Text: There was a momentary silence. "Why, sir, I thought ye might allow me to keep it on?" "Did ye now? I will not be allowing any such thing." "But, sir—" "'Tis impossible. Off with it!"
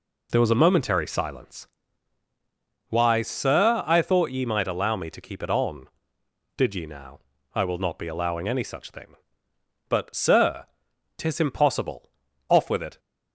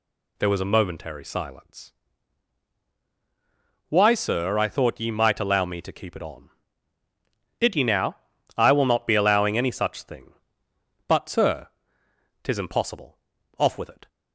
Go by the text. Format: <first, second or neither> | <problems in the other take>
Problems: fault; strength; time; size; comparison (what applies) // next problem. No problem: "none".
neither | none